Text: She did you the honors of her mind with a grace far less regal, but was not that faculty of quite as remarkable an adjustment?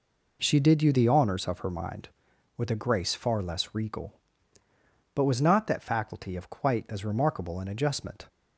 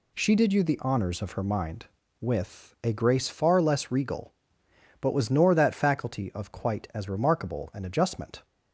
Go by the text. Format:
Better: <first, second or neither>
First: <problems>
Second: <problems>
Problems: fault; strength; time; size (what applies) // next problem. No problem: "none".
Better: first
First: none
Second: says "nor" for "not"; at 5.2 s